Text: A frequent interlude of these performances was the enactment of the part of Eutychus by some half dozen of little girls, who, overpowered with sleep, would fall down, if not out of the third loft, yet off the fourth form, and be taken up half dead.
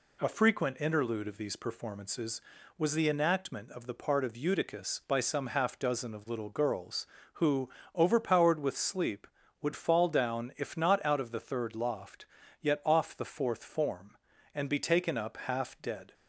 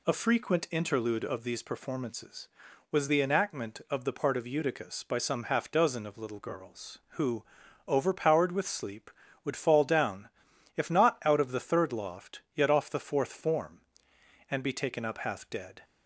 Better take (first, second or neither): neither